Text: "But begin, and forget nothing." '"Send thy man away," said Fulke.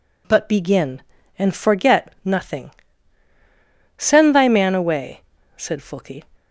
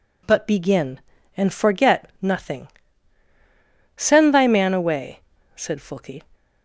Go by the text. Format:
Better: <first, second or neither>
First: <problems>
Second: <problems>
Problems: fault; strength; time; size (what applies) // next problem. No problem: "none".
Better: neither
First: none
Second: none